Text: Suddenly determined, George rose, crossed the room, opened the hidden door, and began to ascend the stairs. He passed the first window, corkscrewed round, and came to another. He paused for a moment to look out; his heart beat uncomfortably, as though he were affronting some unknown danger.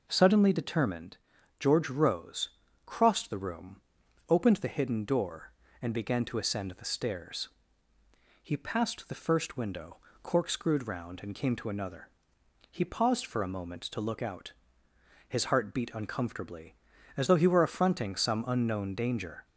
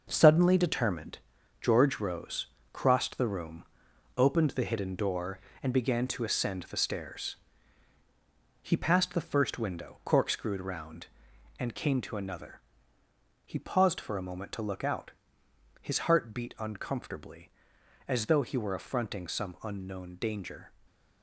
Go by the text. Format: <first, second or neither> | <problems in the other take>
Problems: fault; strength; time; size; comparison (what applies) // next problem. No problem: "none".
first | gets quieter; strong; throughout; 8 dB // stays silent after the last word; slight; from 20.6 s on; 0.6 s long